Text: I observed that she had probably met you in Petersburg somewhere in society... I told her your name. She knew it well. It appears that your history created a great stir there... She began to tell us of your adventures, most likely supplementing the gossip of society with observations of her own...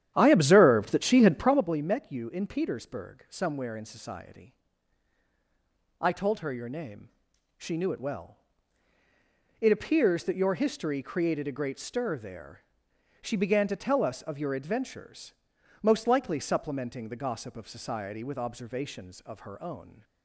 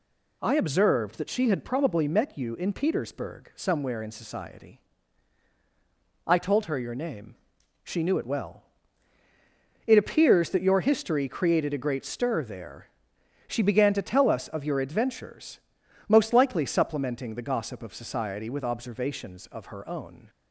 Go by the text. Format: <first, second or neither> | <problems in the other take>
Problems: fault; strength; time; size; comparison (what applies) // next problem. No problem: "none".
second | starts louder than the rest; strong; until 1.6 s; 10.5 dB